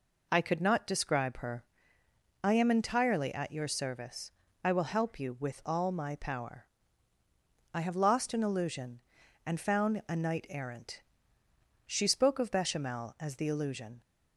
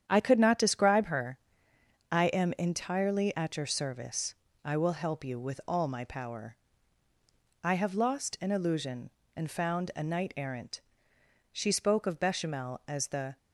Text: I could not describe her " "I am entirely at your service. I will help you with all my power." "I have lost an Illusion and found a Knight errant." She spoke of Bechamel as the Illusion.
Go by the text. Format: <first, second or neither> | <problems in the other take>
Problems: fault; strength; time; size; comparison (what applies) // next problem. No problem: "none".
first | starts louder than the rest; strong; until 1.0 s; 9 dB // stops before "Illusion"; at 13.3 s